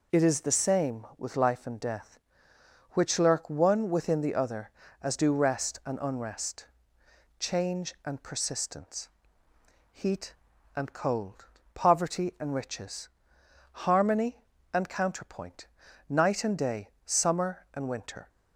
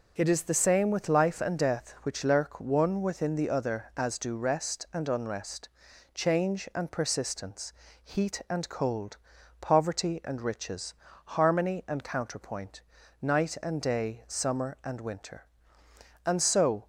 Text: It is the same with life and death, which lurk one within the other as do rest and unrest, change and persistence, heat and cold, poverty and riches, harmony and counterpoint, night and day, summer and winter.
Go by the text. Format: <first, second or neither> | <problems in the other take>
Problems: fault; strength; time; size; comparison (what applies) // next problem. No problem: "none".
first | goes on to say "And so"; noticeable; from 16.2 s on; 0.62 s long